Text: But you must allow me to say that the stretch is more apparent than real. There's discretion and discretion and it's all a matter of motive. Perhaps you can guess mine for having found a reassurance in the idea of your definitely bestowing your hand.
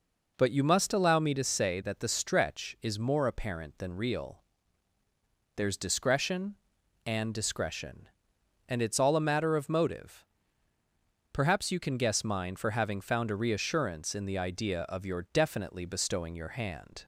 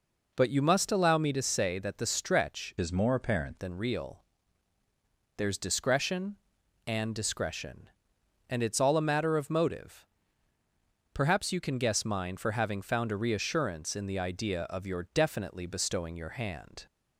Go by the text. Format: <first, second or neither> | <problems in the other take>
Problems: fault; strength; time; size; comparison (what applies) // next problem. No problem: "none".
first | changes voice from "is" to "apparent"; from 2.7 to 3.5 s; 0.8 s long